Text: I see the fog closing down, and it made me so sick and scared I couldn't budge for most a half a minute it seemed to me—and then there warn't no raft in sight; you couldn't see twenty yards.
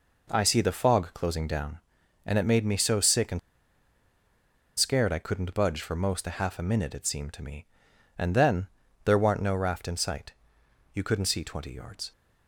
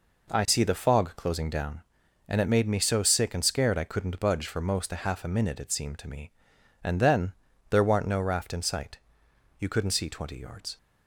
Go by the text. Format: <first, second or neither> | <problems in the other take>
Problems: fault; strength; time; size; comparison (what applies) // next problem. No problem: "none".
second | pauses between "and" and "scared"; strong; at 3.3 s; 1.3 s long // pauses between "then" and "there"; slight; at 8.6 s; 0.36 s long; slight in the second